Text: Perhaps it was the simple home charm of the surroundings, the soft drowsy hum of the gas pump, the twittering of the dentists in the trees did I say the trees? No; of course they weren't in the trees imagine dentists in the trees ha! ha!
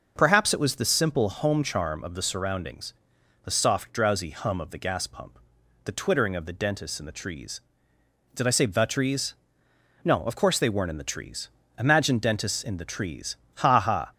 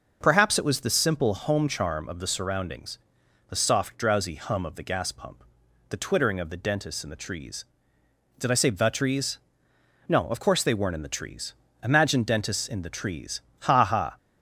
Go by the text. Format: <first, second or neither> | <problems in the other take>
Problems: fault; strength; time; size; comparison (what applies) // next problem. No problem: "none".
neither | pauses between "trees" and "imagine"; slight; the same in both // pauses between "trees" and "ha"; slight; the same in both